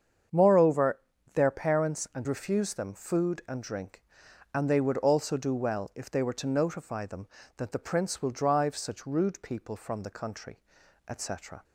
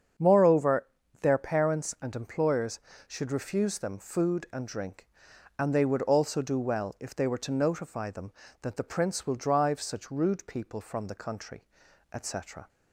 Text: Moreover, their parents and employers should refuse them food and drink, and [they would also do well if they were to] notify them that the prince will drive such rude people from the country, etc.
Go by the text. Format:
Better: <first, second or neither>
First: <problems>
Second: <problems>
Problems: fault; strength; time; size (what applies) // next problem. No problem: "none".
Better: second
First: starts louder than the rest; strong; until 1.6 s; 7.5 dB // skips "employers should"; at 2.2 s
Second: starts louder than the rest; strong; until 1.5 s; 7.5 dB